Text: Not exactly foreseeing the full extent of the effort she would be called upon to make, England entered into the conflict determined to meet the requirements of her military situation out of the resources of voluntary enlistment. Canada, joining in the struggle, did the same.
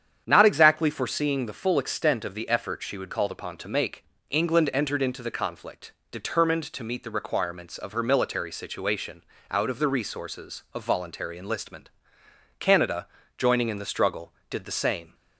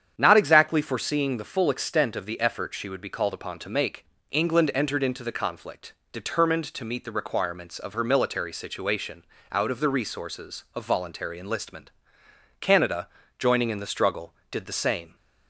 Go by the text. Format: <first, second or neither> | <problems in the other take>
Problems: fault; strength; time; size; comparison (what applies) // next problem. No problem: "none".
second | starts louder than the rest; strong; until 1.2 s; 8.5 dB; strong in the second // skips "be"; at 3.0 s // pauses between "conflict" and "determined"; slight; at 5.9 s; 0.20 s long; slight in the second // pauses between "situation" and "out"; slight; at 9.2 s; 0.26 s long; slight in the second